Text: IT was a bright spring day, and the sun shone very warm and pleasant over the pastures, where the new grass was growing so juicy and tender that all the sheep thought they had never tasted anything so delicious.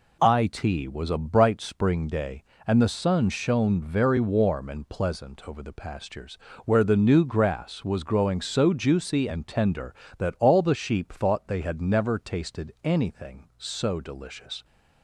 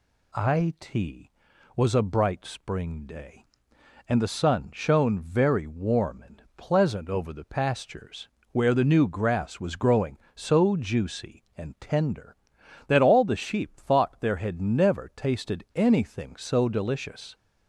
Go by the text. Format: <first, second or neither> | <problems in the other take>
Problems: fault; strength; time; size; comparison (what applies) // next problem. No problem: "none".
first | pauses between "and" and "pleasant"; slight; at 6.4 s; 0.16 s long // says "there" for "they"; at 14.1 s